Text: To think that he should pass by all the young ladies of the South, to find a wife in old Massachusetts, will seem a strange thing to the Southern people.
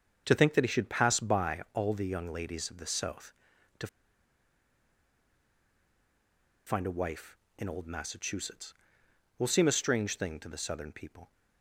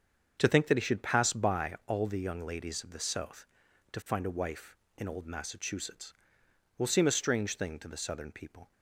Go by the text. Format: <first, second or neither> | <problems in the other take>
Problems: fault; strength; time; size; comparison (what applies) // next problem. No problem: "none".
second | starts louder than the rest; until 1.2 s; 7 dB; also in the second // pauses between "to" and "find"; strong; at 3.8 s; 2.8 s long